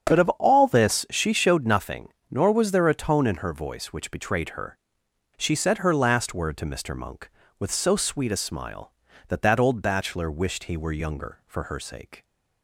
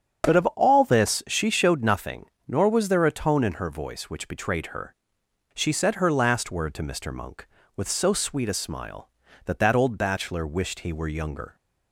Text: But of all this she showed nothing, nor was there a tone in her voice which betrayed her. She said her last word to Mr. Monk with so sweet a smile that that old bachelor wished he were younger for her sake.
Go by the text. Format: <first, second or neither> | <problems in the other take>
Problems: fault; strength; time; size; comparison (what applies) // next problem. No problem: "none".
first | starts louder than the rest; strong; until 1.4 s; 7.5 dB; strong in the first // stops before "for her sake"; at 11.5 s